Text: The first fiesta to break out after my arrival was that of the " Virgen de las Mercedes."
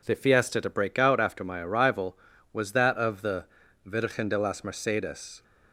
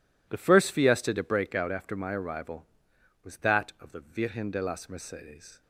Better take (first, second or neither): second